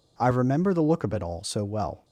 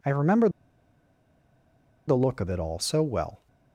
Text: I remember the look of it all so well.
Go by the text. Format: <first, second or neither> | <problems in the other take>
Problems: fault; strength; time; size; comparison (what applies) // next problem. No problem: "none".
first | pauses between "remember" and "the"; strong; at 0.4 s; 1.5 s long